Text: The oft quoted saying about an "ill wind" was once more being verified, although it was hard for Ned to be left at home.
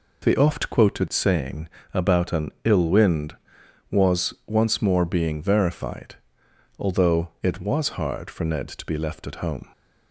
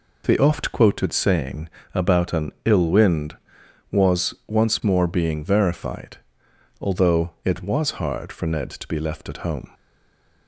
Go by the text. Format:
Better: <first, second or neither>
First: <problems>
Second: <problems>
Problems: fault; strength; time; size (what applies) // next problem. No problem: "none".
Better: first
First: pauses between "saying" and "about"; slight; at 1.6 s; 0.24 s long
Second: pauses between "saying" and "about"; slight; at 1.6 s; 0.24 s long // stays silent after the last word; slight; from 9.7 s on; 0.7 s long